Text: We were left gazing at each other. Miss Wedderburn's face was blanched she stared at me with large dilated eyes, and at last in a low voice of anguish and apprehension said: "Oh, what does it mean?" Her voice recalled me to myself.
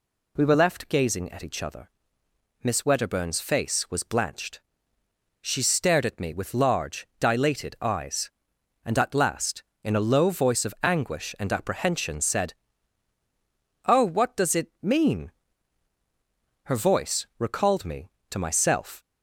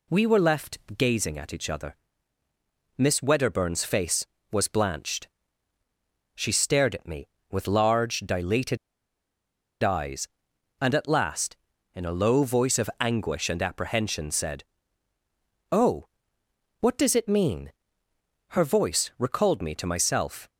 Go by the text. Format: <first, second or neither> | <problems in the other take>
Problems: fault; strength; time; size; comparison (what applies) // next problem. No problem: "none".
first | pauses between "left" and "gazing"; slight; at 0.7 s; 0.20 s long // pauses between "blanched" and "she"; at 5.2 s; 1.0 s long; noticeable in the first // pauses between "dilated" and "eyes"; at 8.7 s; 1.0 s long